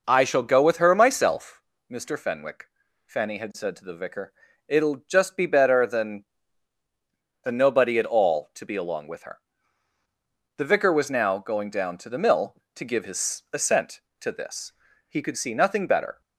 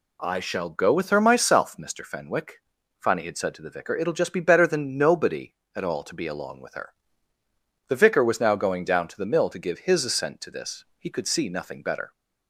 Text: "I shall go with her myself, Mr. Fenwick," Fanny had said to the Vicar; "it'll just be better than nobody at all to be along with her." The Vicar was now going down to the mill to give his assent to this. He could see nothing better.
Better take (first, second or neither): second